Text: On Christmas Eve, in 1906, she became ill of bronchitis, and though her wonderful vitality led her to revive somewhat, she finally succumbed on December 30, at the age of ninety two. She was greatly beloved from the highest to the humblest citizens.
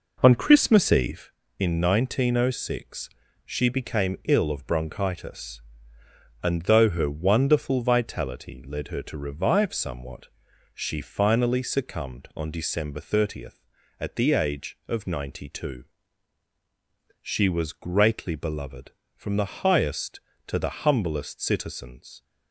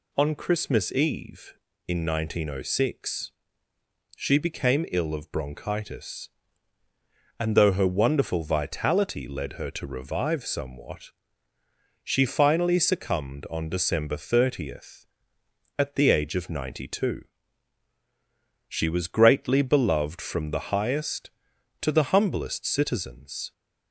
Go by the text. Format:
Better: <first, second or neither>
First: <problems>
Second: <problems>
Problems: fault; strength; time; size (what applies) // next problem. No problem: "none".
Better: second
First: starts louder than the rest; noticeable; until 1.4 s; 4.5 dB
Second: none